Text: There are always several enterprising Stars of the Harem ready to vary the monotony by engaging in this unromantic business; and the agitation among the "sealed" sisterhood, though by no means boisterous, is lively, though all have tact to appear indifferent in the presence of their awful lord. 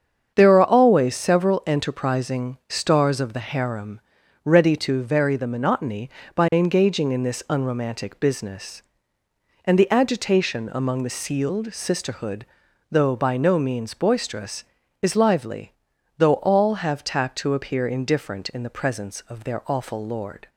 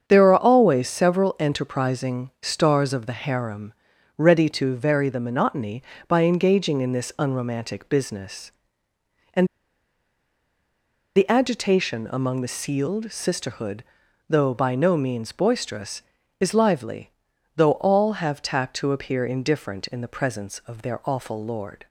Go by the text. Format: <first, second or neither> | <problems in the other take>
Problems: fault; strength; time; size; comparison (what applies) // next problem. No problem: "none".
first | starts louder than the rest; strong; until 1.0 s; 7.5 dB; strong in the first // pauses between "Harem" and "ready"; noticeable; at 3.7 s; 0.46 s long; noticeable in the first // pauses between "and" and "the"; strong; at 9.4 s; 1.6 s long